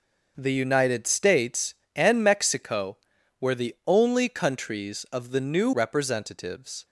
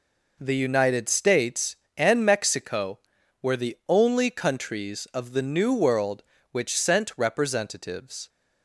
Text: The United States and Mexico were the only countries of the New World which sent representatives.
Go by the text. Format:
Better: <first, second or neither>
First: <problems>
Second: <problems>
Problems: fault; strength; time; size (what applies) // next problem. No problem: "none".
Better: second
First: skips "World which sent"; at 5.7 s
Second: none